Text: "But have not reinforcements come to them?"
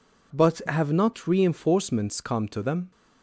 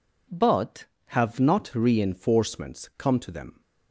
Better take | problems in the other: neither | none

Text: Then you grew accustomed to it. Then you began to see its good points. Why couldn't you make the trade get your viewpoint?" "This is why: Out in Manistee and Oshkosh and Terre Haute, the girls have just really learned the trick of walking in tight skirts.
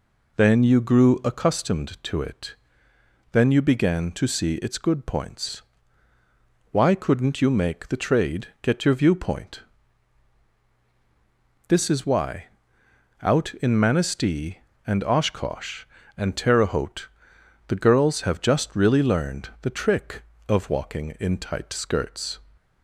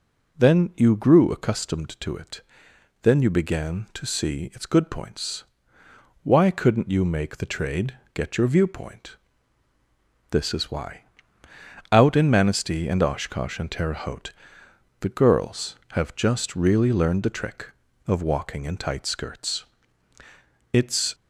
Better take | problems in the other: first | pauses between "trade" and "get"; slight; at 7.9 s; 0.18 s long // goes on to say "It's"; slight; from 20.7 s on; 0.42 s long

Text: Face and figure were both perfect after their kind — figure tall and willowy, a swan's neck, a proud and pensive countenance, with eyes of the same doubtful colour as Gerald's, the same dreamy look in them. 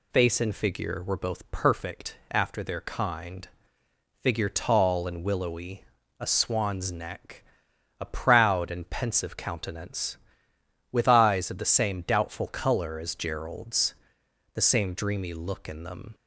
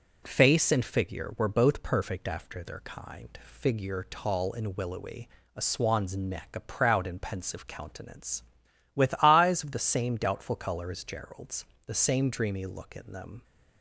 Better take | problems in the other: neither | none

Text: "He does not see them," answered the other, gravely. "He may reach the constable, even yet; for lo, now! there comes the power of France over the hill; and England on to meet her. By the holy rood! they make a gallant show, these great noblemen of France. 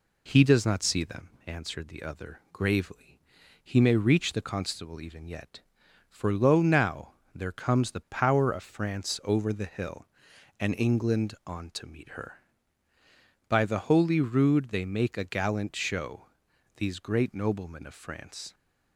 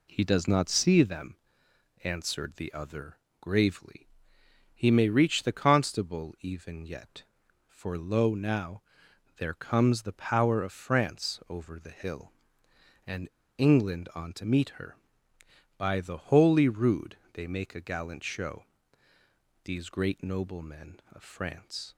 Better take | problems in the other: first | pauses between "and" and "England"; slight; at 13.2 s; 0.28 s long

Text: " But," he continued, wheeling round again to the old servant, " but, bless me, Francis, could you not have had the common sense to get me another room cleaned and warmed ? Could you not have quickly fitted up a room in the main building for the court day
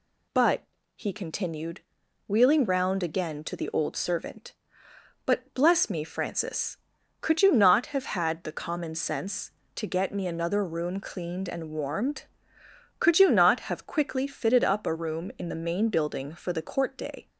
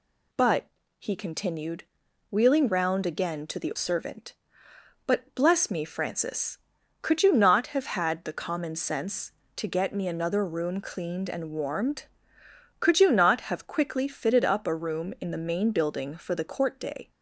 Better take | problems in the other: first | skips "old"; at 3.7 s

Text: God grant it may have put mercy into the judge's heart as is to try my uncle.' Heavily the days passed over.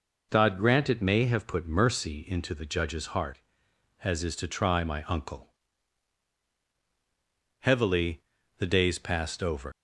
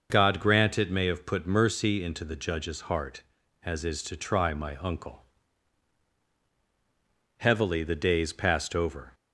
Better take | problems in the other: second | pauses between "Heavily" and "the"; at 8.2 s; 0.38 s long // leaves "over" unfinished; at 9.7 s; 110 ms

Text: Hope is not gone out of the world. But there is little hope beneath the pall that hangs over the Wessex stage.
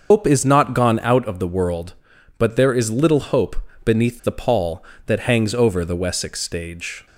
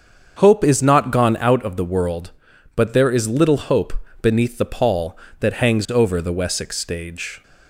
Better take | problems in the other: second | loses the start of "Hope"; at 0.1 s; 110 ms // starts louder than the rest; until 1.1 s; 6 dB; also in the second // pauses between "hope" and "beneath"; slight; at 3.5 s; 0.28 s long; slight in the second

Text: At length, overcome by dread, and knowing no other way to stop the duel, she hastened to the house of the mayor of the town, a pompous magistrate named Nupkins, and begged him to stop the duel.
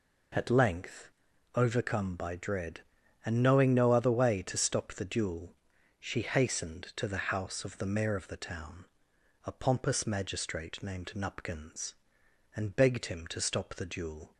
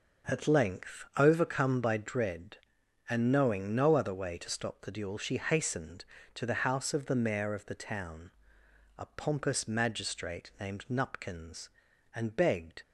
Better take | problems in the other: first | stops before "him to stop the duel"; at 12.8 s

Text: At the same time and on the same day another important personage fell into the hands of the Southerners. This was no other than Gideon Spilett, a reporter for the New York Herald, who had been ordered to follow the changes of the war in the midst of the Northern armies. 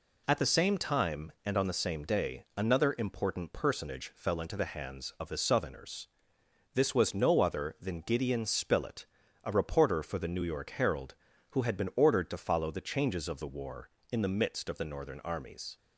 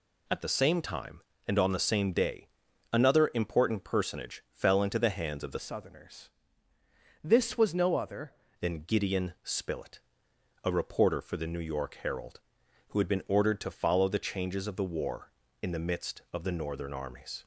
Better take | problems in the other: first | pauses between "day" and "another"; at 2.4 s; 0.44 s long // changes voice from "Southerners" to "other"; from 5.5 to 8.3 s; 2.8 s long

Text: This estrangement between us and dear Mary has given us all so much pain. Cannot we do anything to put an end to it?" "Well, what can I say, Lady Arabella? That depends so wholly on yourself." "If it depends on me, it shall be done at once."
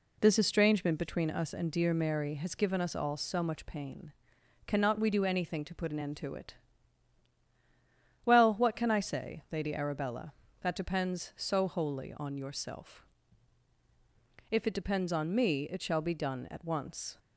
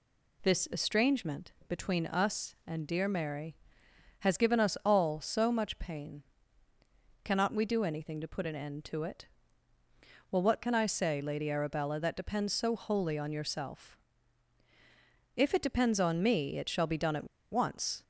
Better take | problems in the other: first | pauses between "estrangement" and "between"; slight; at 1.5 s; 0.16 s long // pauses between "at" and "once"; slight; at 17.2 s; 0.24 s long

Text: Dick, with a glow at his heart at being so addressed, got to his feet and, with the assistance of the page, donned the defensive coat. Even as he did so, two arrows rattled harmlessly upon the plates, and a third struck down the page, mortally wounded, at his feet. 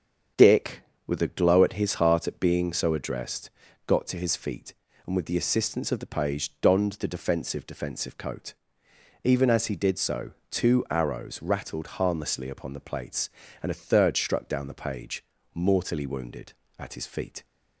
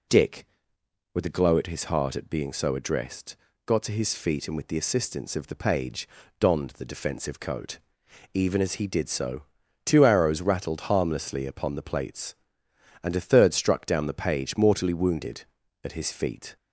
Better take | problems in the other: second | starts louder than the rest; strong; until 1.6 s; 7.5 dB // says "defensive" twice; at 7.6 s

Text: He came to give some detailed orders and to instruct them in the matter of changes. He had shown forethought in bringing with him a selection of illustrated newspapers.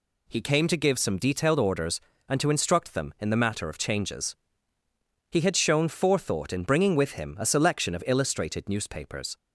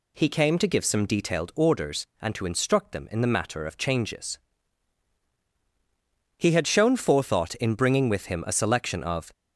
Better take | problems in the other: first | stops before "illustrated newspapers"; at 9.3 s

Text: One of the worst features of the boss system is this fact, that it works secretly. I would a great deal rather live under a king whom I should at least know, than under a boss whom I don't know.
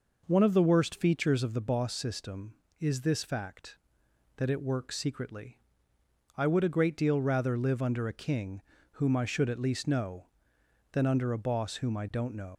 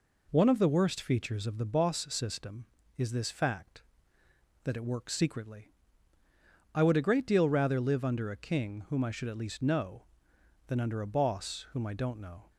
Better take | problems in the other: second | pauses between "king" and "whom"; slight; at 8.6 s; 0.30 s long // leaves "know" unfinished; at 12.5 s; 110 ms

